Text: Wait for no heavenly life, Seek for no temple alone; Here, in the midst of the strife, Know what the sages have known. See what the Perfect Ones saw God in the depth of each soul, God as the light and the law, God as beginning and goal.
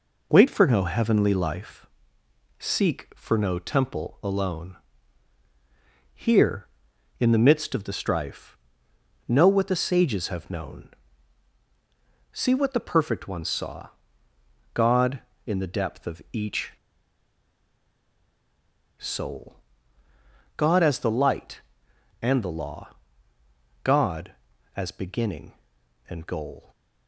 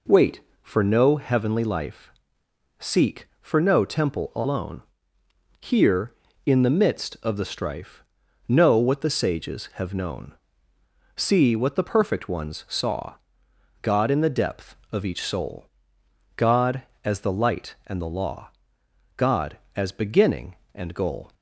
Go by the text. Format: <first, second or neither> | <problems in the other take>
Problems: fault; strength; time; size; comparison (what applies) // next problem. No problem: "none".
second | pauses between "saw" and "God"; noticeable; at 13.8 s; 0.84 s long; noticeable in the second // pauses between "each" and "soul"; strong; at 16.7 s; 2.2 s long